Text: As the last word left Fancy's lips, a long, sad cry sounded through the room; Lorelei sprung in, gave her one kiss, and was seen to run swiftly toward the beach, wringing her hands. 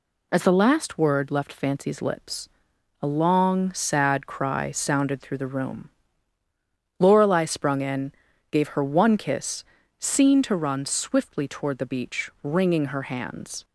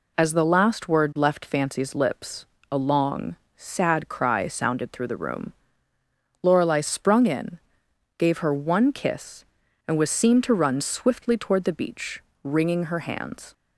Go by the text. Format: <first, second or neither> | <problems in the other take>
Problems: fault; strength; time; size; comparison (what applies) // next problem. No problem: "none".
second | skips "and was"; at 9.8 s